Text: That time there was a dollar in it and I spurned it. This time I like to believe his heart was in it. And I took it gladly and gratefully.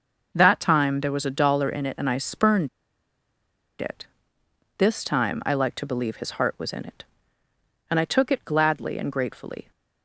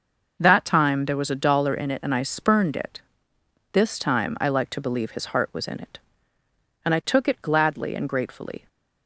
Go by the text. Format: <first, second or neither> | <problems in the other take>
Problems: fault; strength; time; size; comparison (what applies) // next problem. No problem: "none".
second | pauses between "spurned" and "it"; at 2.6 s; 1.1 s long